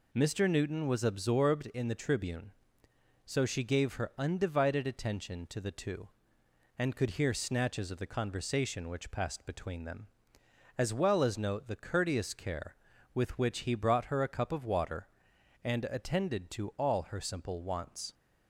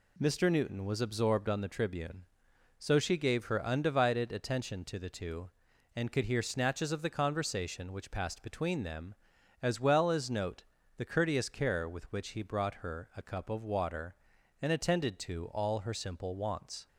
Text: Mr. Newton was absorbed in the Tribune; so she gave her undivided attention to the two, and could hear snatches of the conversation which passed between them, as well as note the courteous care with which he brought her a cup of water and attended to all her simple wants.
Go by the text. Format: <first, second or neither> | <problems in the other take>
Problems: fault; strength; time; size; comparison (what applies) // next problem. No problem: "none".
first | says "on" for "in"; at 1.4 s // pauses between "note" and "the"; slight; at 10.6 s; 0.34 s long